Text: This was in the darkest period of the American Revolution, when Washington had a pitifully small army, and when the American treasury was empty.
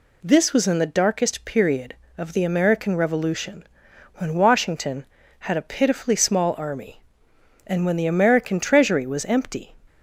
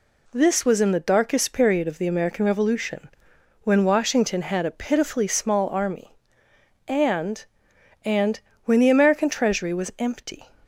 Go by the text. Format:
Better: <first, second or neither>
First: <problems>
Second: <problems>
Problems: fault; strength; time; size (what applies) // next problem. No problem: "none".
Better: first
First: none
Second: says "and" twice; at 8.0 s